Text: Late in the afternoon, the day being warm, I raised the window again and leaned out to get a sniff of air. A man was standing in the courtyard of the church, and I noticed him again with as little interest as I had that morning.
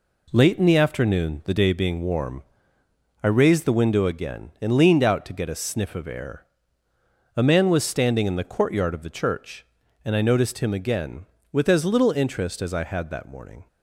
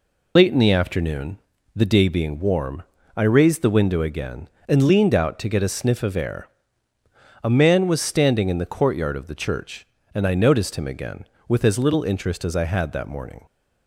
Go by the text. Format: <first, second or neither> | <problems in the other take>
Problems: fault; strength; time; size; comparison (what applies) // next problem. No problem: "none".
first | loses the start of "Late"; at 0.3 s; 50 ms